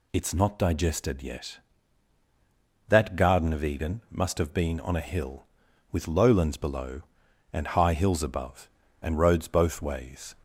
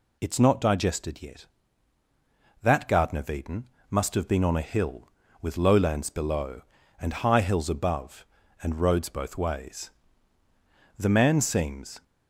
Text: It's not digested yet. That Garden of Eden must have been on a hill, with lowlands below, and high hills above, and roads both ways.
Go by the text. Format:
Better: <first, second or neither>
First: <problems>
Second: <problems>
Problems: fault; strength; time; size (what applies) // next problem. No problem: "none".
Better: first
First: none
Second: pauses between "Eden" and "must"; slight; at 3.6 s; 0.26 s long // goes on to say "The man seems"; noticeable; from 10.9 s on; 1.0 s long